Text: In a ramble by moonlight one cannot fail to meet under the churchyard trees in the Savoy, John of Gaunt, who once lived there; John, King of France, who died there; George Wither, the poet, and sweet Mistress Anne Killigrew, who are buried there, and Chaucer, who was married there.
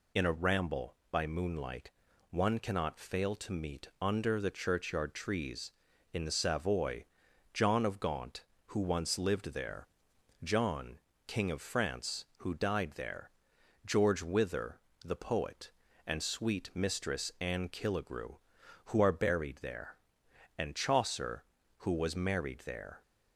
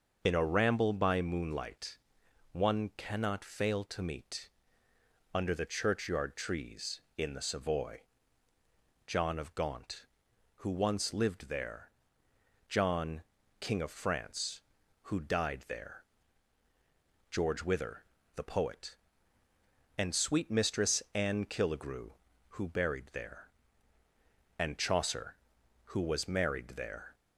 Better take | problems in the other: first | starts louder than the rest; until 1.2 s; 6 dB // pauses between "moonlight" and "one"; noticeable; at 1.9 s; 0.54 s long; also in the first // pauses between "meet" and "under"; noticeable; at 4.4 s; 0.86 s long // skips "are"; at 22.6 s

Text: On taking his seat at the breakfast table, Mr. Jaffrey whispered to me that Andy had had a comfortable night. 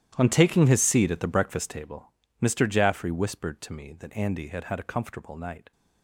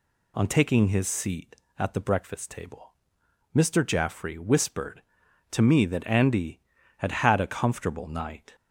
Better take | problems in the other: second | gets quieter; strong; throughout; 17.5 dB

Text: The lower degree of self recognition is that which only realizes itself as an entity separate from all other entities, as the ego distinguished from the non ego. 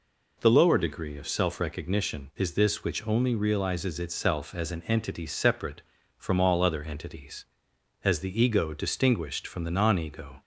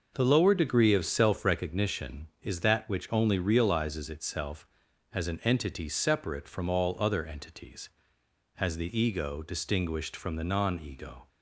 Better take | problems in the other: second | says "this" for "that"; at 2.5 s

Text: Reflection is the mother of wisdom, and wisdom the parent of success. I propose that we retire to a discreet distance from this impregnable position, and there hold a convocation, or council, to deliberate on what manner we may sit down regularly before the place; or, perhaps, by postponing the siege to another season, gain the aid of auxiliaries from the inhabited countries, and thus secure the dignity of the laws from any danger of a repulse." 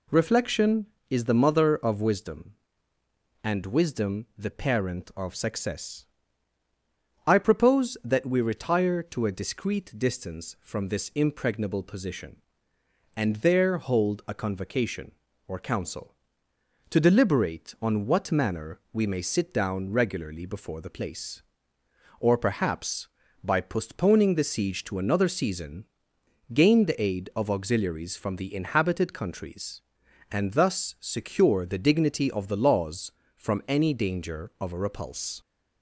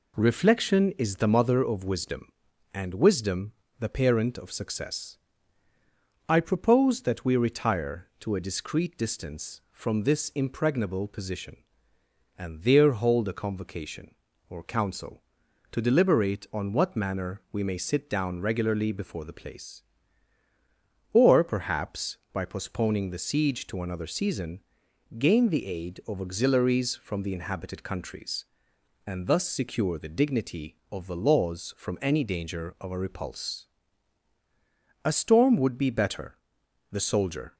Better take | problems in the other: first | pauses between "wisdom" and "the"; slight; at 3.5 s; 0.30 s long // goes on to say "A storm would be better the soldier"; strong; from 35.0 s on; 2.5 s long

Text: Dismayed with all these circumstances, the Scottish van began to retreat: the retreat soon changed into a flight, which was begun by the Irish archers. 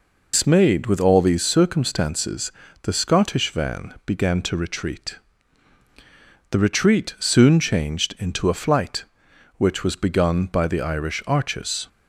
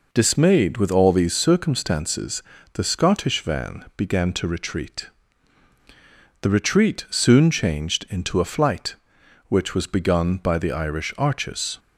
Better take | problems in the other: second | loses the start of "Dismayed"; at 0.3 s; 115 ms

